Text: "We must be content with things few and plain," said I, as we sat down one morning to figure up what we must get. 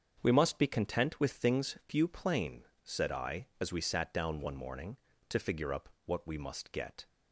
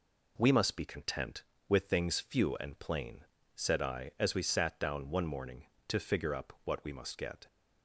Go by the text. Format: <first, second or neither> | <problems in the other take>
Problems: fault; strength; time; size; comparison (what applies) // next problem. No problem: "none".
second | starts louder than the rest; until 1.2 s; 7 dB // skips "and"; at 2.0 s // pauses between "up" and "what"; slight; at 5.8 s; 0.18 s long